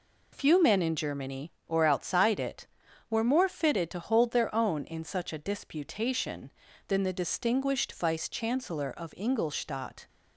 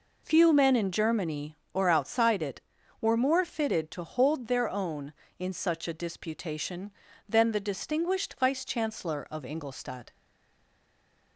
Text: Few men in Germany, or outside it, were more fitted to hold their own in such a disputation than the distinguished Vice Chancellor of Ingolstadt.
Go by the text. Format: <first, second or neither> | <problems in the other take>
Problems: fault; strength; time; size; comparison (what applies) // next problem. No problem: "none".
first | stays silent after the last word; noticeable; from 10.1 s on; 1.2 s long